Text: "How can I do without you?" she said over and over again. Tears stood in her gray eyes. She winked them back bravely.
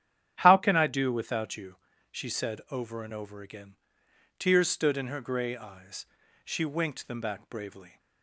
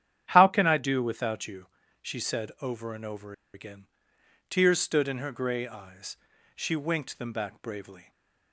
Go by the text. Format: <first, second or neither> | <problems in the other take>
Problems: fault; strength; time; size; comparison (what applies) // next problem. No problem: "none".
first | starts louder than the rest; strong; until 1.3 s; 10 dB; strong in the first // pauses between "over" and "again"; slight; at 3.3 s; 0.21 s long // stays silent after the last word; slight; from 8.0 s on; 0.5 s long